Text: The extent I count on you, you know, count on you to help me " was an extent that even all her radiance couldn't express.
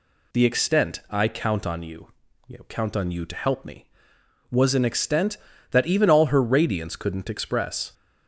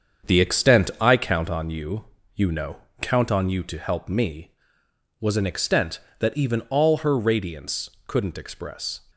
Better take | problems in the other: first | gets quieter; strong; throughout; 7.5 dB // pauses between "radiance" and "couldn't"; slight; at 7.8 s; 0.18 s long

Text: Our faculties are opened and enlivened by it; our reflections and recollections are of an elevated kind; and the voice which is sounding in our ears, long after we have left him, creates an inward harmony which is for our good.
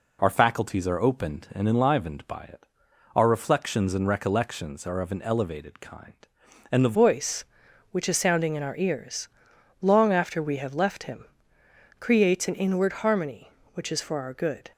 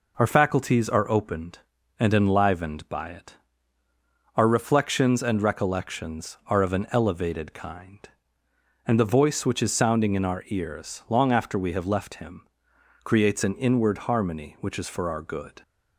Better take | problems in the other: second | changes voice at "voice"; from 6.9 s on; 7.8 s long

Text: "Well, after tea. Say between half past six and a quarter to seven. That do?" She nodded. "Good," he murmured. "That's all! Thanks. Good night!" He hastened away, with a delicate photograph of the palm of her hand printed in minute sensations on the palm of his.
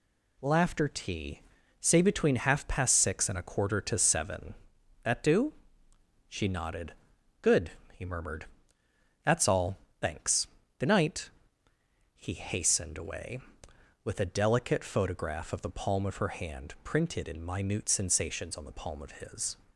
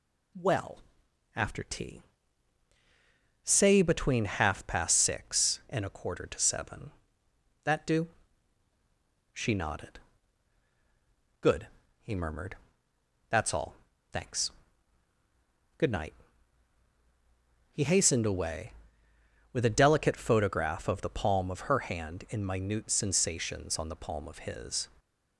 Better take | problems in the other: first | skips "printed"; at 22.2 s

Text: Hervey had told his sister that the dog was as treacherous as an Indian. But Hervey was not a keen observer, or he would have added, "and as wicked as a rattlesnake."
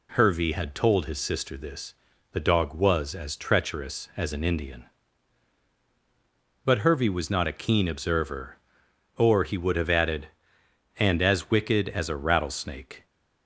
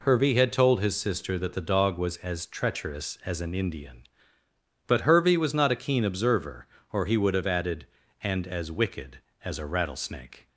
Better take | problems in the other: second | says "this" for "that"; at 1.5 s

